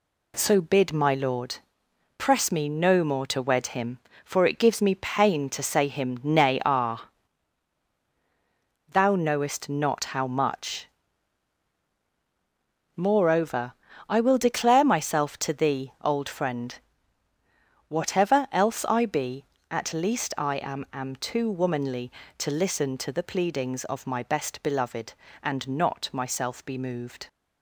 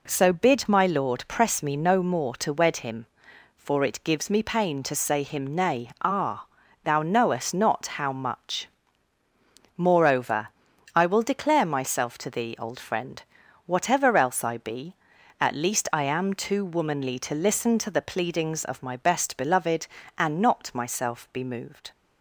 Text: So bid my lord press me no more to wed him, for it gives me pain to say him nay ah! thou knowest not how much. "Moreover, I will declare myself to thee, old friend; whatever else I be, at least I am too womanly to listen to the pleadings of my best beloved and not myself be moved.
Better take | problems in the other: second | pauses between "lord" and "press"; noticeable; at 1.5 s; 0.62 s long // says "am" twice; at 20.9 s

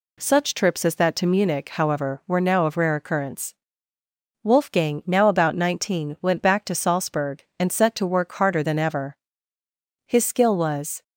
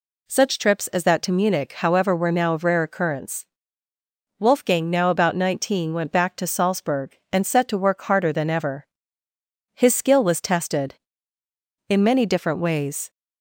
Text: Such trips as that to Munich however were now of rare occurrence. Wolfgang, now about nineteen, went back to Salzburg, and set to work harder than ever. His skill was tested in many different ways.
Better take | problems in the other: second | stops before "tested in many different ways"; at 11.0 s

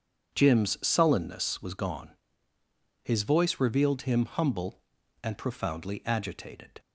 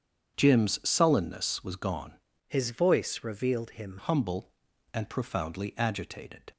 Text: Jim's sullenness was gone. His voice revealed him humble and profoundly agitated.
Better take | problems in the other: first | starts louder than the rest; strong; until 1.3 s; 8 dB; strong in the first // changes voice from "His" to "him"; from 2.4 to 3.9 s; 1.5 s long

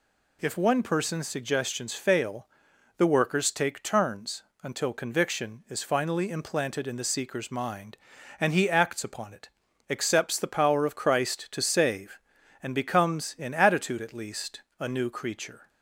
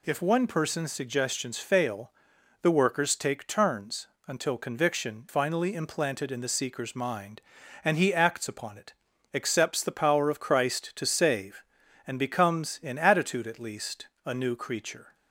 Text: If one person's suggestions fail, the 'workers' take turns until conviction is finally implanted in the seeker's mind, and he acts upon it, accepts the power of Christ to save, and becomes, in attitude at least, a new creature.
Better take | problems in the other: first | pauses between "turns" and "until"; slight; at 4.0 s; 0.20 s long; slight in the first // skips "is"; at 5.2 s

